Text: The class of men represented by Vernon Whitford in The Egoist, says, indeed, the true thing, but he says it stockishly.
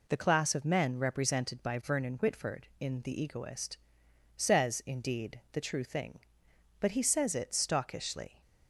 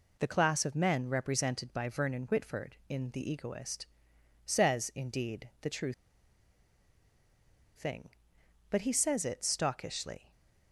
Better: first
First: none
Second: pauses between "true" and "thing"; strong; at 5.9 s; 1.8 s long

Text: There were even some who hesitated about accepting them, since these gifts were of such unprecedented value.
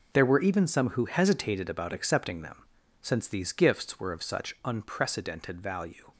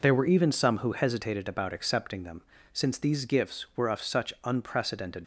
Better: first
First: none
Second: stops before "value"; at 5.2 s

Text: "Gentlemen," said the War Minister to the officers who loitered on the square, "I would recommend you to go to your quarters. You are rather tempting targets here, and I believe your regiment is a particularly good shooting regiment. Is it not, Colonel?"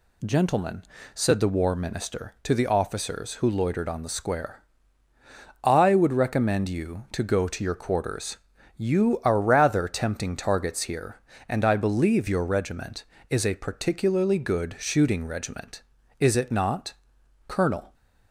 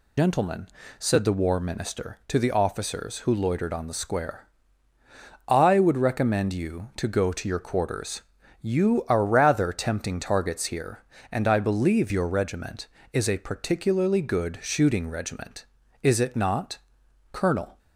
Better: first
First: none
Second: loses the start of "Gentlemen"; at 0.1 s; 110 ms

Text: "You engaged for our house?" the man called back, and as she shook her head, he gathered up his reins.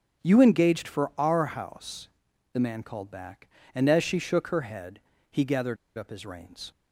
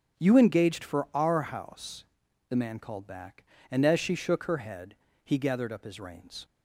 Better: second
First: starts louder than the rest; until 1.2 s; 7 dB // pauses between "gathered" and "up"; slight; at 5.7 s; 0.22 s long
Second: starts louder than the rest; until 1.2 s; 7 dB

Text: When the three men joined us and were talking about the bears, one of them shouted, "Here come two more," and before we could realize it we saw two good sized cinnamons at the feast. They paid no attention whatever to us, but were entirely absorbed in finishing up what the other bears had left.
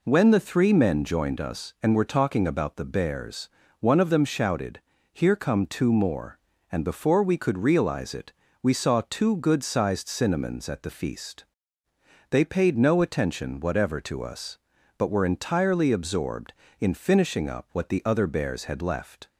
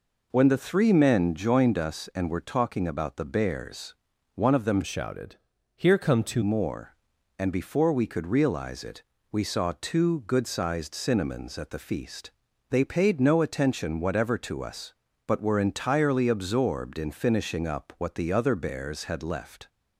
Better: first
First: pauses between "it" and "we"; slight; at 8.3 s; 0.30 s long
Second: changes voice from "shouted" to "two"; from 4.8 to 6.4 s; 1.6 s long // pauses between "it" and "we"; slight; at 9.0 s; 0.30 s long

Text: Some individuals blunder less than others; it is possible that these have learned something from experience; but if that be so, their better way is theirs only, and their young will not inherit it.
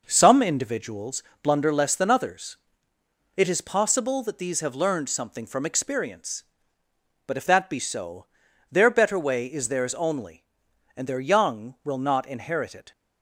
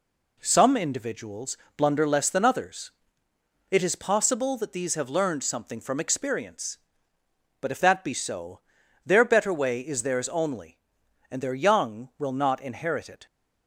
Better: second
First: starts louder than the rest; noticeable; until 1.2 s; 5.5 dB // pauses between "individuals" and "blunder"; slight; at 1.2 s; 0.18 s long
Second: pauses between "individuals" and "blunder"; slight; at 1.5 s; 0.18 s long

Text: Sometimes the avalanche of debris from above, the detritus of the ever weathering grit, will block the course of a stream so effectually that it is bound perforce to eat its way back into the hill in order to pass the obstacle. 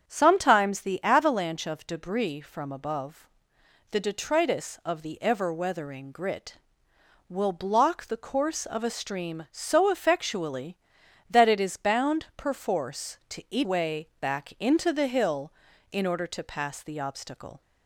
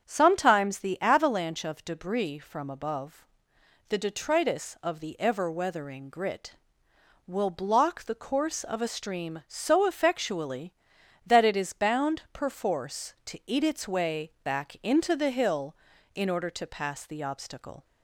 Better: second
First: starts louder than the rest; strong; until 1.0 s; 7.5 dB // skips "its"; at 13.6 s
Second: starts louder than the rest; strong; until 1.0 s; 7.5 dB

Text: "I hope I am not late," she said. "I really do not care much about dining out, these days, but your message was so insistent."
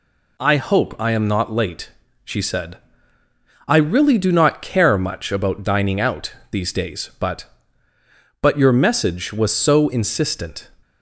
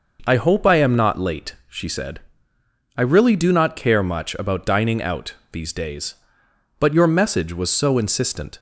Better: second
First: says "but" twice; at 8.4 s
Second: none

